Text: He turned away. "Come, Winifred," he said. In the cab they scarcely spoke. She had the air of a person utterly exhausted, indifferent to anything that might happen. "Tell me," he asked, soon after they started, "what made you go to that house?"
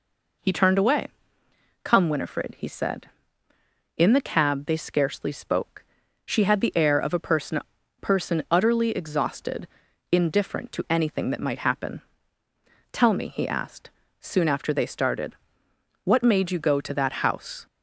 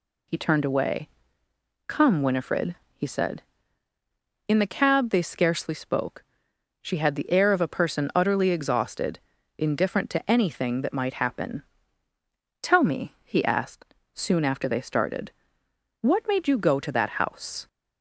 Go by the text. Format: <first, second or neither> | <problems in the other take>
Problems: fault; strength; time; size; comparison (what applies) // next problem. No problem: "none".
second | says "person" twice; at 7.9 s